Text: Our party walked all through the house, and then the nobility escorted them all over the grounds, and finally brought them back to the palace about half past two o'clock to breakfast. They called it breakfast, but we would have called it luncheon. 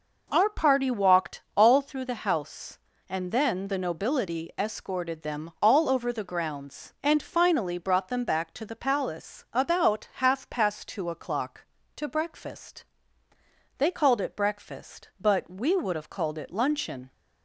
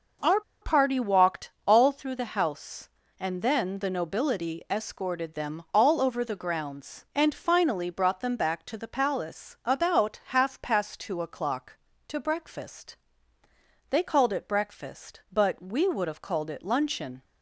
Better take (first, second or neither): first